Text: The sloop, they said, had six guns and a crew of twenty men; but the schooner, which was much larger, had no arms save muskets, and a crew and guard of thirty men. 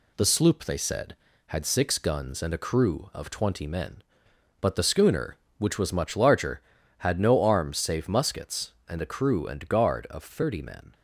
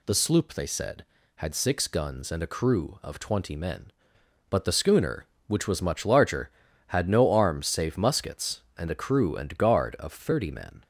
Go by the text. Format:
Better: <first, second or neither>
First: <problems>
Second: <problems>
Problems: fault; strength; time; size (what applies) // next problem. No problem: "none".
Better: second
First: gets quieter; slight; throughout; 2.5 dB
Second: none